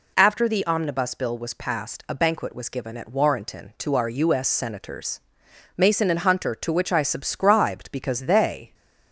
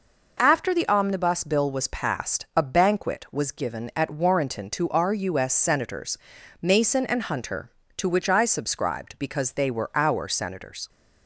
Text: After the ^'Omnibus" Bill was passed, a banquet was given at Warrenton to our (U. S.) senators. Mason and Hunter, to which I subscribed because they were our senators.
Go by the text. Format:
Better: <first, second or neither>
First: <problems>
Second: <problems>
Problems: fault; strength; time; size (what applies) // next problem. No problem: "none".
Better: second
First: stops before "were our senators"; at 8.7 s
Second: none